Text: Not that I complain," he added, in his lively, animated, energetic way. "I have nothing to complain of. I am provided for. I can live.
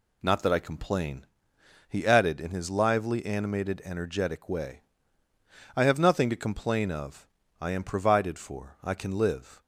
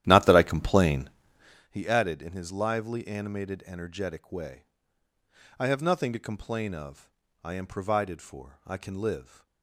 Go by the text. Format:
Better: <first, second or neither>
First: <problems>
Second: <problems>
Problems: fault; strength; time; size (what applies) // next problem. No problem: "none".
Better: first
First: none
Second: starts louder than the rest; strong; until 1.7 s; 12.5 dB